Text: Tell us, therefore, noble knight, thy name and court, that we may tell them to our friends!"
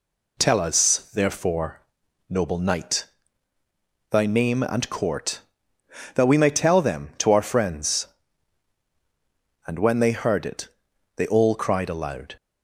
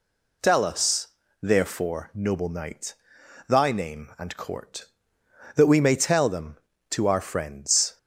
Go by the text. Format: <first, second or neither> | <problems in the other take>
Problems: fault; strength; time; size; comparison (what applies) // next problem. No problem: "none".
second | goes on to say "And when they heard it they all cried aloud"; strong; from 9.6 s on; 2.7 s long